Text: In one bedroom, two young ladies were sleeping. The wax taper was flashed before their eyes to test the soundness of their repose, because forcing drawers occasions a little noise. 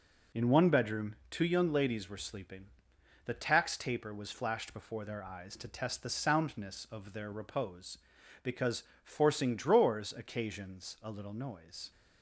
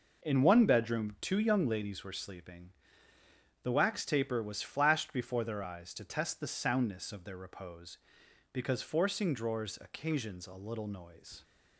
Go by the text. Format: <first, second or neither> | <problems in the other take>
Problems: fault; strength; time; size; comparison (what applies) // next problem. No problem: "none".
second | says "tax" for "wax"; at 3.3 s // pauses between "because" and "forcing"; slight; at 8.8 s; 0.22 s long